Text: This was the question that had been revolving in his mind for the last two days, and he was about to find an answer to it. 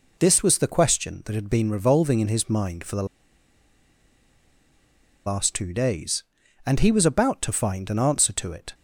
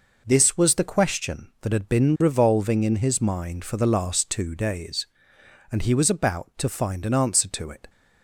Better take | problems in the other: second | pauses between "the" and "last"; strong; at 3.0 s; 2.2 s long

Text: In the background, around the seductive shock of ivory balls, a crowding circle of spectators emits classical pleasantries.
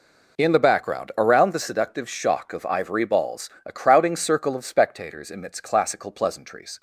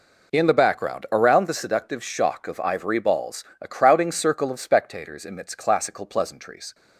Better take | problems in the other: neither | none

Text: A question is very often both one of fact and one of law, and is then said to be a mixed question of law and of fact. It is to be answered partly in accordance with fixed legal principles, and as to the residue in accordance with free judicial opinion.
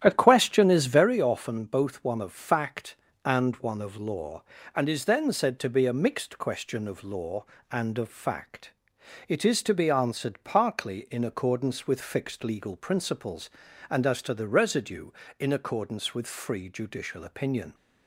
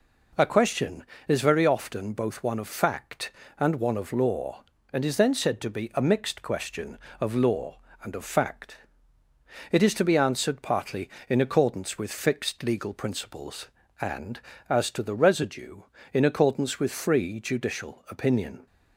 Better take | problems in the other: second | starts louder than the rest; strong; until 1.1 s; 11 dB

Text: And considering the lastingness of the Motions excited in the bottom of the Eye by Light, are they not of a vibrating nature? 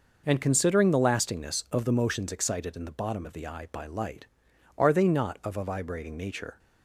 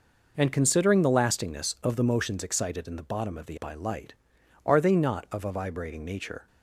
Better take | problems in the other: first | skips "Eye"; at 3.5 s

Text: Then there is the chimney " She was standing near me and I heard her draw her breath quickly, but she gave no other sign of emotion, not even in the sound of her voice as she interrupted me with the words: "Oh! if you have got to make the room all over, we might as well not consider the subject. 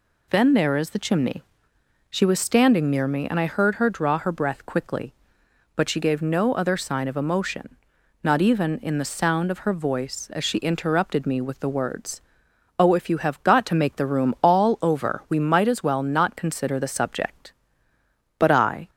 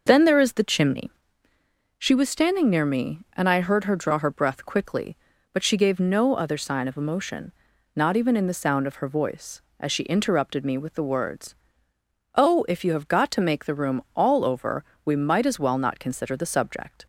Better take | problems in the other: second | goes on to say "But I"; from 18.3 s on; 0.52 s long

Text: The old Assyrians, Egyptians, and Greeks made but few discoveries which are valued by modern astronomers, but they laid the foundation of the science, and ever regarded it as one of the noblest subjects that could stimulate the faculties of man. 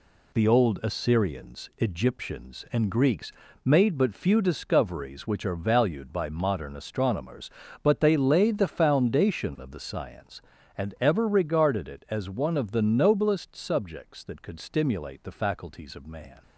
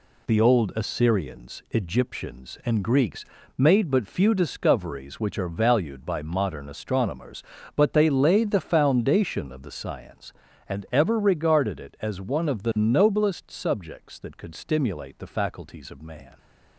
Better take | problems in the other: neither | pauses between "Greeks" and "made"; slight; the same in both

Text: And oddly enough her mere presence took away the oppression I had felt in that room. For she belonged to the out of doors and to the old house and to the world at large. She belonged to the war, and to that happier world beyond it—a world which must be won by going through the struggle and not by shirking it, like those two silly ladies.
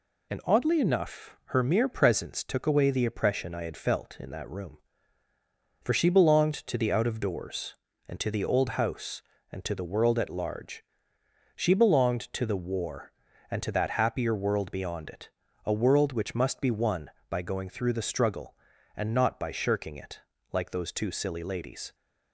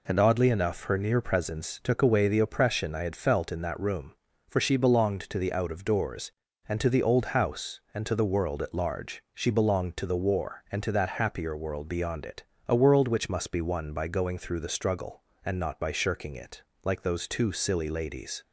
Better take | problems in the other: first | says "near" for "mere"; at 0.9 s

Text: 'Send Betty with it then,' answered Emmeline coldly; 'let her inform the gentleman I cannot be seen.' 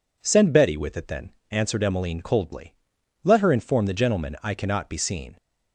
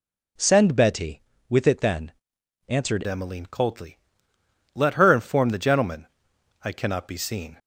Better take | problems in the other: first | changes voice at "Emmeline"; from 3.0 s on; 4.5 s long // pauses between "gentleman" and "I"; noticeable; at 6.0 s; 0.56 s long

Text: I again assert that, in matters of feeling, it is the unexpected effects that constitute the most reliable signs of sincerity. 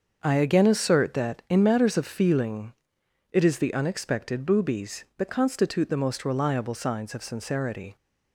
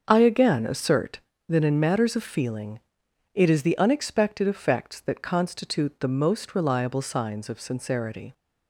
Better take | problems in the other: second | starts louder than the rest; until 1.2 s; 6.5 dB; also in the second // says "boobies" for "effects"; at 4.4 s

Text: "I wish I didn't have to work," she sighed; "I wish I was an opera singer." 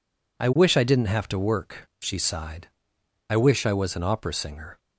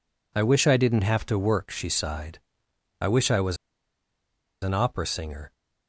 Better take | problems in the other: first | pauses between "was" and "an"; at 3.5 s; 1.0 s long

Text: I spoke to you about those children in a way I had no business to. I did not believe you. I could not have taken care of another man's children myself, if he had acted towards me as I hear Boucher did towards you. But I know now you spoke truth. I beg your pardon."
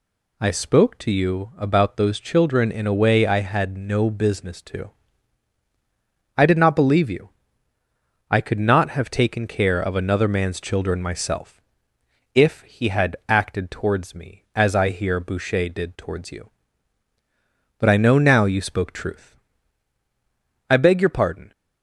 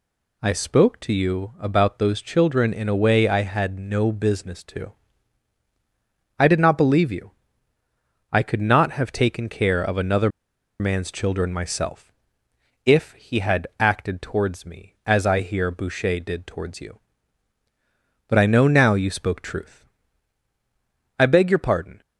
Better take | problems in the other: first | pauses between "another" and "man's"; noticeable; at 10.2 s; 0.50 s long

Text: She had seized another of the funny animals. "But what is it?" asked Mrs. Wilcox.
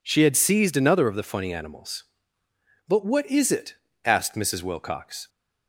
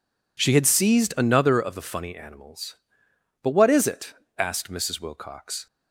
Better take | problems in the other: neither | none

